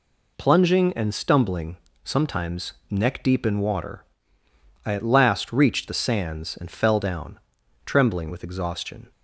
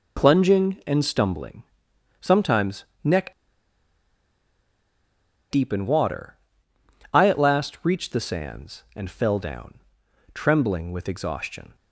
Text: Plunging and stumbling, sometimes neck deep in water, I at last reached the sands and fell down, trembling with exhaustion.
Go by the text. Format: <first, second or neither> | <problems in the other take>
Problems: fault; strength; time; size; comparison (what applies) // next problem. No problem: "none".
first | pauses between "sometimes" and "neck"; slight; at 2.8 s; 0.18 s long; slight in the first // pauses between "neck" and "deep"; strong; at 3.3 s; 2.1 s long